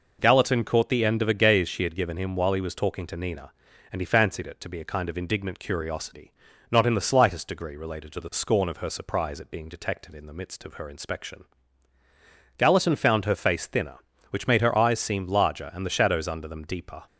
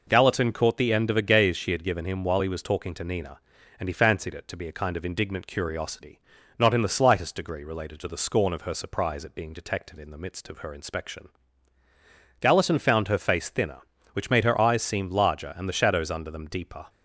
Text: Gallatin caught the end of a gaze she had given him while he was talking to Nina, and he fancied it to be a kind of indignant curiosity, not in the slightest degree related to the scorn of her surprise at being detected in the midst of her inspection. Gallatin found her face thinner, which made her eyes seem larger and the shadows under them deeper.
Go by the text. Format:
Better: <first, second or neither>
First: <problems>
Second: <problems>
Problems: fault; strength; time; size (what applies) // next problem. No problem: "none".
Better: neither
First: none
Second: none